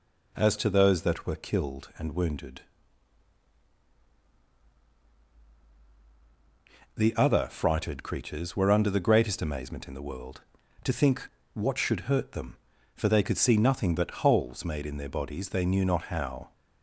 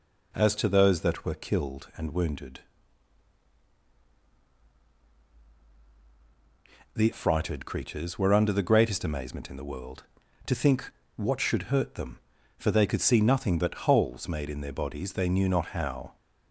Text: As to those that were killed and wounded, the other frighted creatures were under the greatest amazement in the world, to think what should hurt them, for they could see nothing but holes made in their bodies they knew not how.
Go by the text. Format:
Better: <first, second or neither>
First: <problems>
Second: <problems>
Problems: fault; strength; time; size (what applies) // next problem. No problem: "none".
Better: first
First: pauses between "think" and "what"; slight; at 11.2 s; 0.26 s long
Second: skips "other"; at 7.1 s // pauses between "think" and "what"; slight; at 10.8 s; 0.26 s long